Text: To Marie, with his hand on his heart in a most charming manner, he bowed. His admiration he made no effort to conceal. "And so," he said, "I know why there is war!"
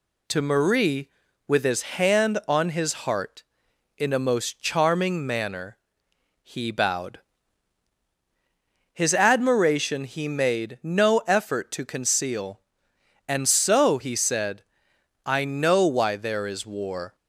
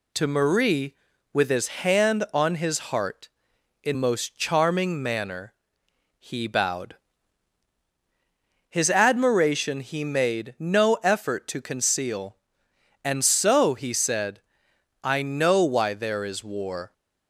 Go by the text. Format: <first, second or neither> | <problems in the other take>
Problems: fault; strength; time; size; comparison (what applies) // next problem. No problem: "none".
first | skips "a"; at 3.9 s